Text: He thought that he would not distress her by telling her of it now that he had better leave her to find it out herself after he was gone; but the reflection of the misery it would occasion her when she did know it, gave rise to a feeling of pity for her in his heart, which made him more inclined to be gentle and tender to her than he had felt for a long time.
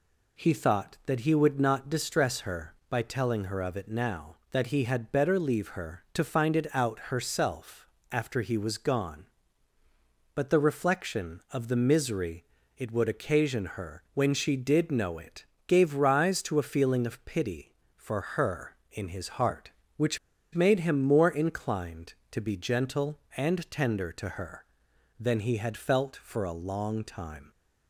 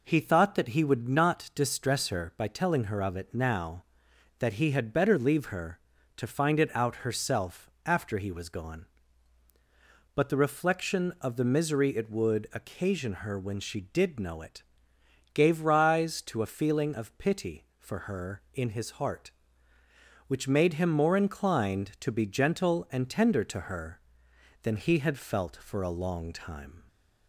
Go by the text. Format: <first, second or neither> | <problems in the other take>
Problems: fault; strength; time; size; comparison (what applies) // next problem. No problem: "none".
second | pauses between "herself" and "after"; slight; at 7.8 s; 0.24 s long; slight in the second // pauses between "misery" and "it"; slight; at 12.4 s; 0.32 s long // pauses between "which" and "made"; at 20.1 s; 0.36 s long